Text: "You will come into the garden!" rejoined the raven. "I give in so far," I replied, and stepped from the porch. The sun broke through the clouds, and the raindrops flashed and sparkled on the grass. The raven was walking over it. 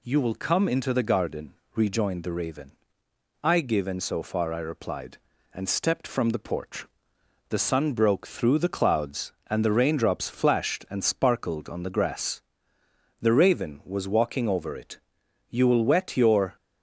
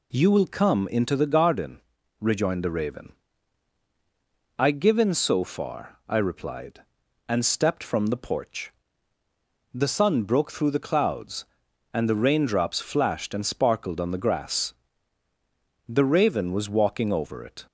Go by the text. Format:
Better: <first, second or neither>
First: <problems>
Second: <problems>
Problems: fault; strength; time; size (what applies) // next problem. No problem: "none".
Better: second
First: goes on to say "You will wet your"; noticeable; from 15.4 s on; 1.0 s long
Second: none